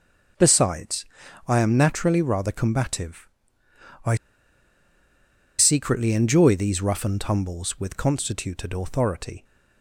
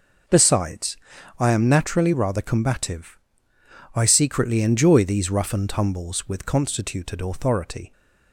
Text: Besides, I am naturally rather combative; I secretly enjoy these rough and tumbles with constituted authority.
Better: second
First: pauses between "I" and "secretly"; strong; at 4.1 s; 1.4 s long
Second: none

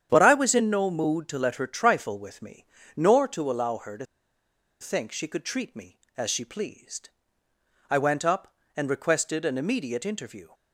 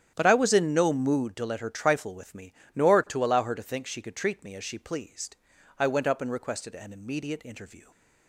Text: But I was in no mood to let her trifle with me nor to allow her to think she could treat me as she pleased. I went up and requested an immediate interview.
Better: second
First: starts louder than the rest; strong; until 1.1 s; 9 dB // pauses between "me" and "nor"; slight; at 2.6 s; 0.32 s long // pauses between "to" and "think"; noticeable; at 4.0 s; 0.76 s long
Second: starts louder than the rest; strong; until 1.1 s; 10 dB // pauses between "me" and "nor"; slight; at 2.5 s; 0.22 s long

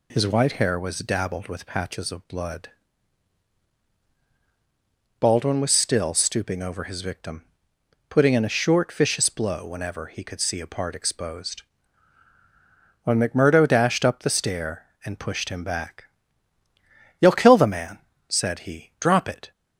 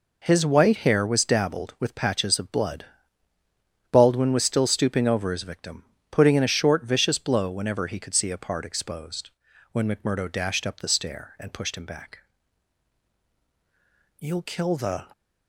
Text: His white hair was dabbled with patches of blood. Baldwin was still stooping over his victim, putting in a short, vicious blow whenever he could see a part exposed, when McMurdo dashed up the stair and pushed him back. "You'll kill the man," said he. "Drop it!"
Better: first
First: none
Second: stops before "man said he Drop it"; at 15.1 s

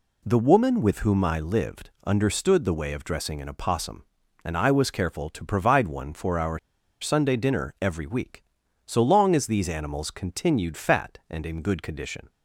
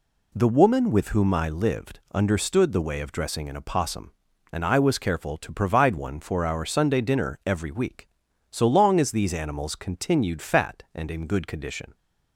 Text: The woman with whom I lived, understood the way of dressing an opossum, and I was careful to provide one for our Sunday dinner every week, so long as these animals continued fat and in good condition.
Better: second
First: pauses between "our" and "Sunday"; at 6.5 s; 0.42 s long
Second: none

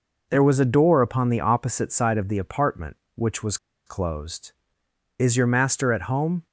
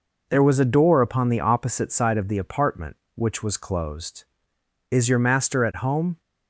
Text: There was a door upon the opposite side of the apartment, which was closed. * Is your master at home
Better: second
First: pauses between "was" and "closed"; slight; at 3.5 s; 0.30 s long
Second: none

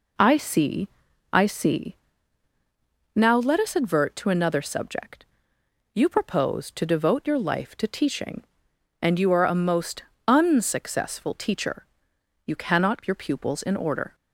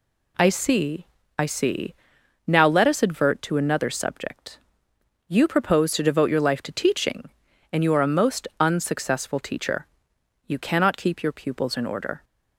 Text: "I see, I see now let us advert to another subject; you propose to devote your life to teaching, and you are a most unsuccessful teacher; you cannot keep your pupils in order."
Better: second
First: pauses between "see" and "now"; at 1.9 s; 1.1 s long // pauses between "most" and "unsuccessful"; slight; at 10.0 s; 0.22 s long // skips "keep"; at 13.0 s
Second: pauses between "see" and "now"; noticeable; at 1.9 s; 0.52 s long

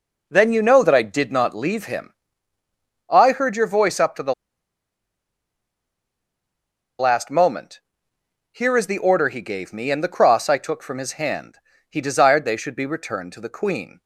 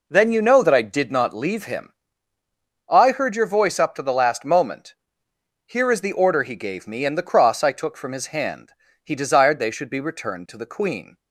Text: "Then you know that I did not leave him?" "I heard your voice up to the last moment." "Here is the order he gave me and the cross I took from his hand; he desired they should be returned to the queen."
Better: second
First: pauses between "the" and "last"; strong; at 4.3 s; 2.6 s long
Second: none

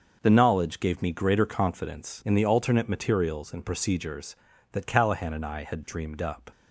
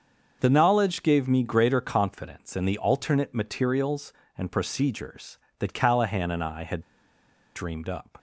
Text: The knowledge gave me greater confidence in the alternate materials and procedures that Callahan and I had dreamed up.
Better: first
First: starts louder than the rest; until 1.2 s; 6 dB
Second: starts louder than the rest; until 1.4 s; 6.5 dB // pauses between "had" and "dreamed"; noticeable; at 6.8 s; 0.74 s long

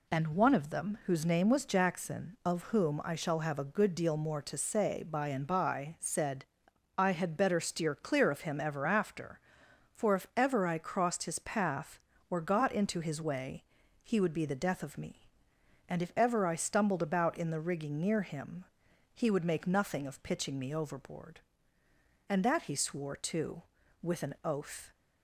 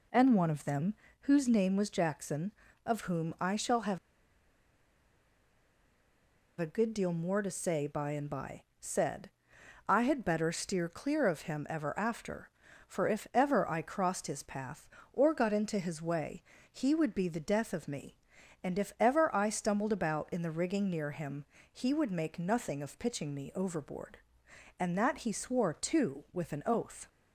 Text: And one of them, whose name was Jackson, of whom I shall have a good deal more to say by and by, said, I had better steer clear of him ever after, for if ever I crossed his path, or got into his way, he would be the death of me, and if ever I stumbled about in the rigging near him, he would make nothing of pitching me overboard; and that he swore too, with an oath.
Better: first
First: none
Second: pauses between "have" and "a"; strong; at 3.9 s; 2.6 s long

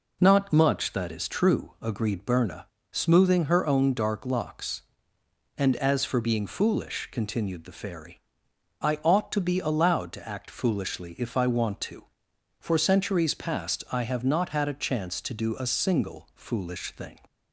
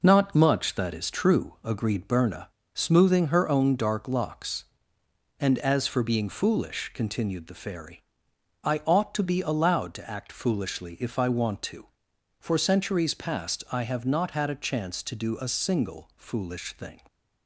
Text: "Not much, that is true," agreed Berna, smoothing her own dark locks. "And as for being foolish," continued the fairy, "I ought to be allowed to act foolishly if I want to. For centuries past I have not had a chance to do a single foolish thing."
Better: first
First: none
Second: gets quieter; throughout; 6 dB

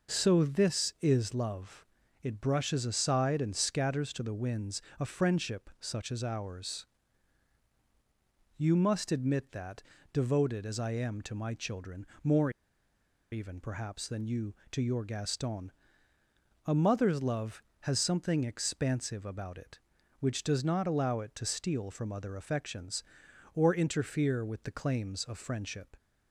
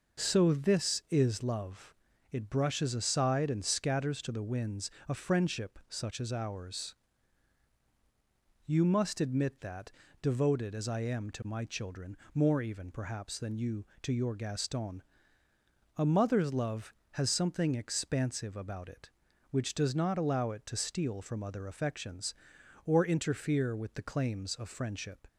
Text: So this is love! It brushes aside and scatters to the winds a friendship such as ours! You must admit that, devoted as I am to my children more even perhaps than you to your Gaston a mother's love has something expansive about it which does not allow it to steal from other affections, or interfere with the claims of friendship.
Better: second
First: pauses between "winds" and "a"; slight; at 4.8 s; 0.16 s long // pauses between "children" and "more"; slight; at 12.0 s; 0.16 s long // pauses between "more" and "even"; noticeable; at 12.4 s; 0.82 s long // pauses between "Gaston" and "a"; noticeable; at 15.7 s; 0.94 s long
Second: pauses between "winds" and "a"; slight; at 4.9 s; 0.16 s long // pauses between "children" and "more"; slight; at 12.1 s; 0.16 s long // pauses between "Gaston" and "a"; noticeable; at 15.0 s; 0.94 s long

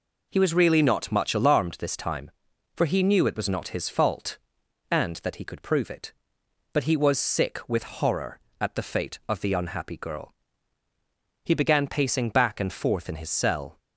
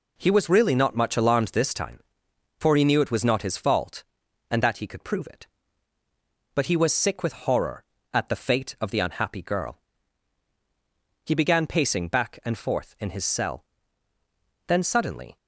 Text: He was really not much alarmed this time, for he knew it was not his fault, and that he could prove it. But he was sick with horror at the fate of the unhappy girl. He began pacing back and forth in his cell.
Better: first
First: none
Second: goes on to say "Then suddenly"; noticeable; from 14.6 s on; 0.70 s long

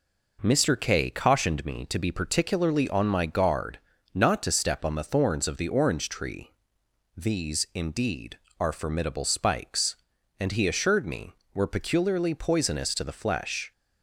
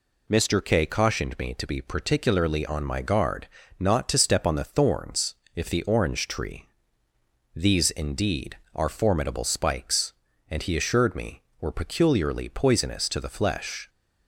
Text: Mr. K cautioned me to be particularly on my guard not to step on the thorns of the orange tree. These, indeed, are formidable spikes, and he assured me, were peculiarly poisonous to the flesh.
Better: first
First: pauses between "guard" and "not"; slight; at 3.7 s; 0.36 s long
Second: pauses between "guard" and "not"; slight; at 3.4 s; 0.32 s long // says "if" for "of"; at 5.5 s

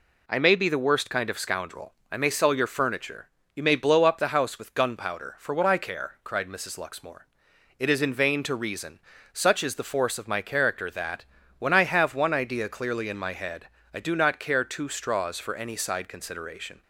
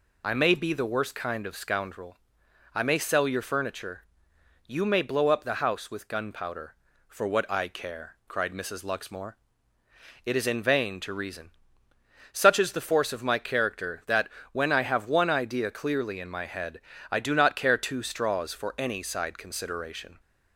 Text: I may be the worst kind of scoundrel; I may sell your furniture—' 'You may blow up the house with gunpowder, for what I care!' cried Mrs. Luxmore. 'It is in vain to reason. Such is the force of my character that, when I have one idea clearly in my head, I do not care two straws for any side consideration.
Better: first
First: none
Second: loses the start of "I"; at 0.2 s; 25 ms

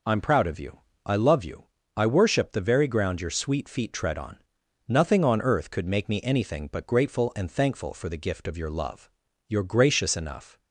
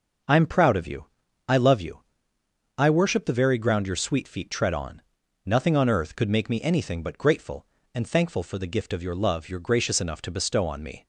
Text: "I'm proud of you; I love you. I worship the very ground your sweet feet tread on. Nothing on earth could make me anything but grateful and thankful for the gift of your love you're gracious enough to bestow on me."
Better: second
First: pauses between "love" and "you're"; at 9.0 s; 0.42 s long // stops before "to bestow on me"; at 10.5 s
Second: none

